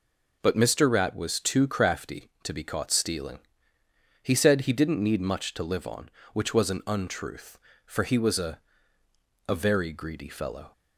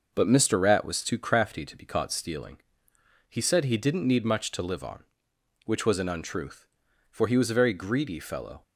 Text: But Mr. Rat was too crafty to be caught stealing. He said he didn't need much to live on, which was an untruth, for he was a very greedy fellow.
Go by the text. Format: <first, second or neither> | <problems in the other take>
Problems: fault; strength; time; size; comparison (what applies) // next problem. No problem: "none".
second | says "a" twice; at 9.4 s